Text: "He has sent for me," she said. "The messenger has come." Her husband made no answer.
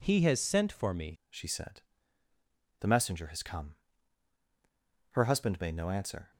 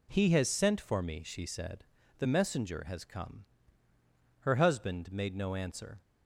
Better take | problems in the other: second | changes voice at "she"; from 1.2 s on; 5.1 s long

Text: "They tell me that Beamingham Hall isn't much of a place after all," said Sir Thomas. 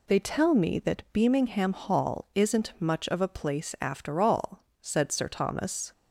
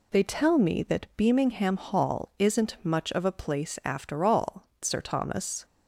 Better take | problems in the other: first | skips "said"; at 4.7 s

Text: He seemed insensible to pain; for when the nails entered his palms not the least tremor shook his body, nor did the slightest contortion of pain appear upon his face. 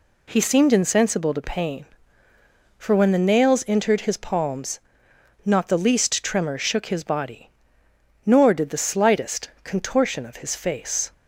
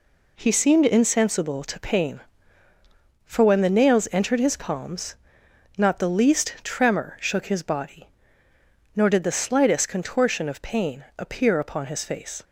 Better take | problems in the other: second | pauses between "palms" and "not"; noticeable; at 4.7 s; 0.64 s long; noticeable in the second // skips "pain appear upon"; at 10.4 s

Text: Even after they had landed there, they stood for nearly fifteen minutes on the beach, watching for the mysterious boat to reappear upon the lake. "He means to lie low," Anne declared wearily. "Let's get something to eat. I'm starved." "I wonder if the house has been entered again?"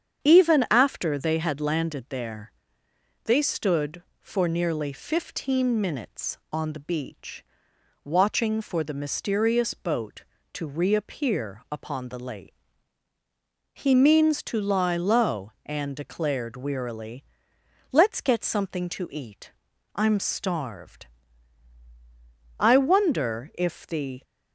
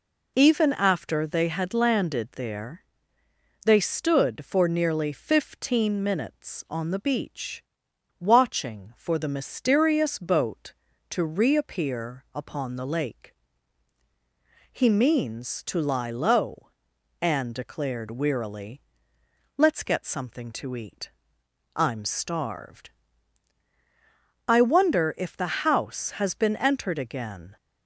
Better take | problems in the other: second | starts louder than the rest; strong; until 1.2 s; 8 dB // stops before "house has been entered again"; at 24.2 s

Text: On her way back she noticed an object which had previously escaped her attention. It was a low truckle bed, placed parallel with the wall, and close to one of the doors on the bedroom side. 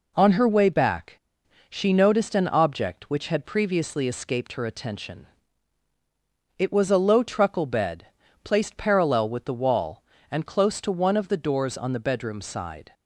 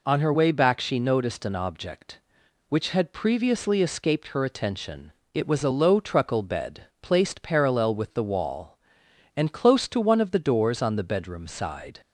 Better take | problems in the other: second | pauses between "back" and "she"; noticeable; at 1.1 s; 0.51 s long

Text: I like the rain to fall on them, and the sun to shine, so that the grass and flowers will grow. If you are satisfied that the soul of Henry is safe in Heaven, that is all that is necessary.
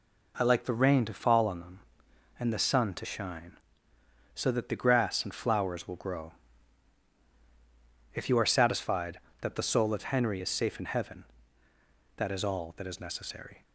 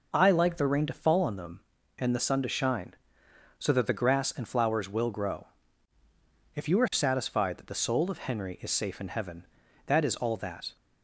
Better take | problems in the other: first | stops before "is necessary"; at 10.7 s

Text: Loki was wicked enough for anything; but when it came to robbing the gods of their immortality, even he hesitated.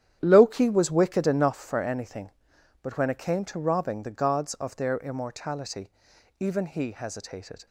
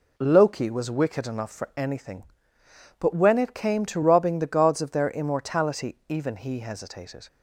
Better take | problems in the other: second | starts louder than the rest; strong; until 1.6 s; 10 dB

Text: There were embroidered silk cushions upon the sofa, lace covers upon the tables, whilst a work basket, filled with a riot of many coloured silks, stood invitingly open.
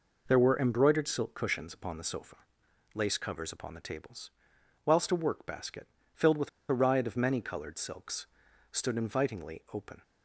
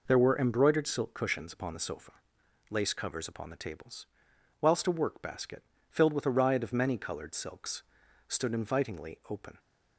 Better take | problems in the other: second | pauses between "with" and "a"; slight; at 6.4 s; 0.21 s long

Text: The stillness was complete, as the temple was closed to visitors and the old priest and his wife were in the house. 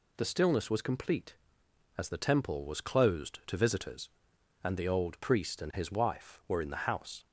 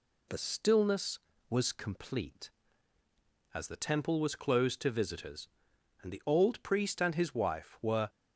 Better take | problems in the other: first | stops before "in the house"; at 8.0 s

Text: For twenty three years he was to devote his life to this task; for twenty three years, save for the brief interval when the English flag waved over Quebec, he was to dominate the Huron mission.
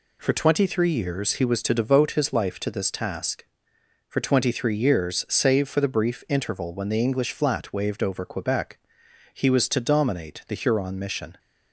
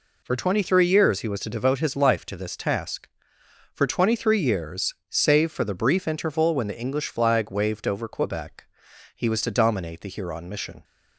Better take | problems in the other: second | says "flat" for "flag"; at 7.3 s

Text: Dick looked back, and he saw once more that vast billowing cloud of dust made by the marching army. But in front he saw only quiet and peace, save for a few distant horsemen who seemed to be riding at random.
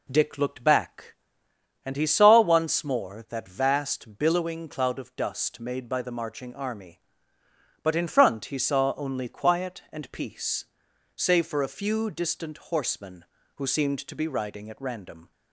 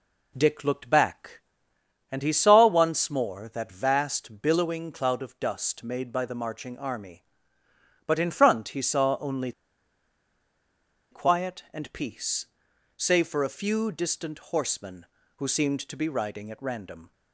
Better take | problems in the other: first | pauses between "only" and "quiet"; strong; at 9.5 s; 1.5 s long

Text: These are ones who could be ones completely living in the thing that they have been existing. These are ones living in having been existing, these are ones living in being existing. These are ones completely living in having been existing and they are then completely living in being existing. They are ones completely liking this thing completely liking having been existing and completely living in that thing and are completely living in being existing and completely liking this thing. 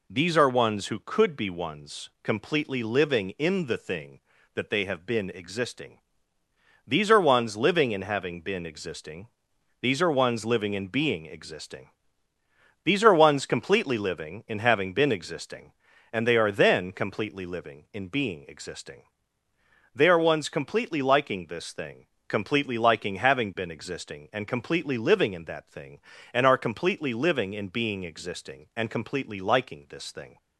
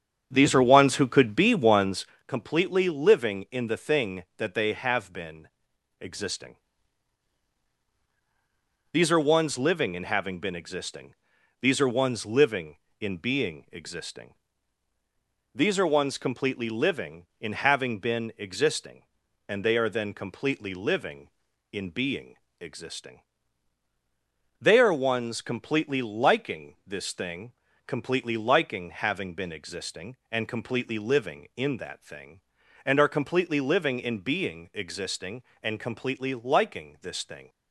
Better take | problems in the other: first | starts louder than the rest; strong; until 2.2 s; 7.5 dB // pauses between "ones" and "completely"; slight; at 2.0 s; 0.20 s long // pauses between "been" and "existing"; noticeable; at 5.4 s; 0.52 s long // pauses between "being" and "existing"; slight; at 22.3 s; 0.26 s long // pauses between "thing" and "completely"; slight; at 27.5 s; 0.36 s long; slight in the first

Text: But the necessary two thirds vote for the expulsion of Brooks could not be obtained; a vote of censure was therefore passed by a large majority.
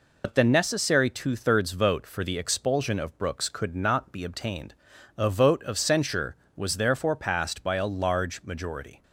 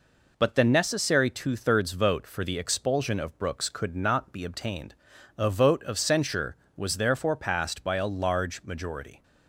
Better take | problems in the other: second | loses the start of "But"; at 0.2 s; 80 ms

